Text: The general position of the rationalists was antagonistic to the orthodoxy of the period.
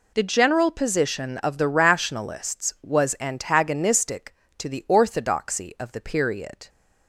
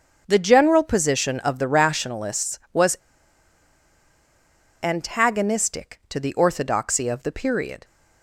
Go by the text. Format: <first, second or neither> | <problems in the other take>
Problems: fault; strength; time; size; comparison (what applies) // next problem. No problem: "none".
first | starts louder than the rest; until 1.2 s; 7 dB // pauses between "was" and "antagonistic"; strong; at 2.9 s; 1.8 s long